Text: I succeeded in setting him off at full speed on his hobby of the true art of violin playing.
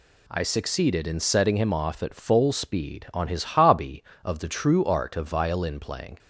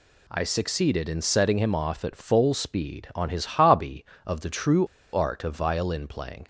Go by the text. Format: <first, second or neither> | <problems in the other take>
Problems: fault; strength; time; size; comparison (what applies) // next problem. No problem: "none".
first | pauses between "true" and "art"; slight; at 4.8 s; 0.28 s long